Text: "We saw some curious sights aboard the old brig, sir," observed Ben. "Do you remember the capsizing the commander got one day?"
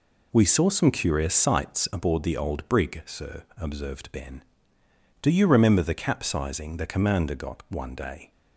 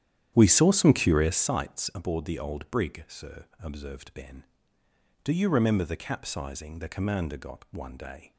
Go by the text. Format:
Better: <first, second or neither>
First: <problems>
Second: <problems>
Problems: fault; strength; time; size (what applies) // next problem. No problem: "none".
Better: first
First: none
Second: starts louder than the rest; strong; until 1.4 s; 10.5 dB